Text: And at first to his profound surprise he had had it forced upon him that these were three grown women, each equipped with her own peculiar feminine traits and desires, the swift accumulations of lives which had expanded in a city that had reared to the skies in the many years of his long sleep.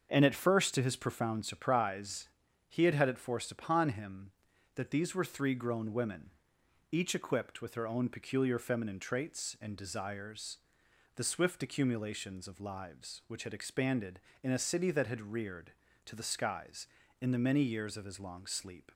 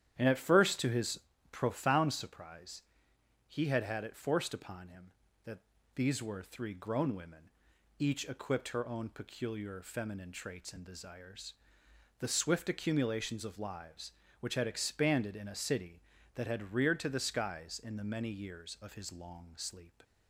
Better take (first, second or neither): first